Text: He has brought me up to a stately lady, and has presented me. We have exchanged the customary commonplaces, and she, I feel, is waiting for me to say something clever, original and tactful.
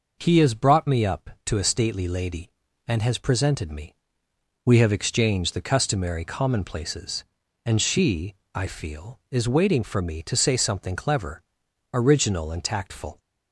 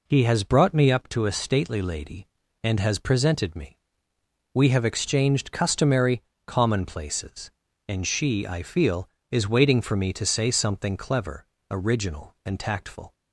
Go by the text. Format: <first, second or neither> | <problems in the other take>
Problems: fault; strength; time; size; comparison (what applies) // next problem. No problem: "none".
first | skips "the"; at 5.5 s // pauses between "customary" and "commonplaces"; slight; at 6.2 s; 0.24 s long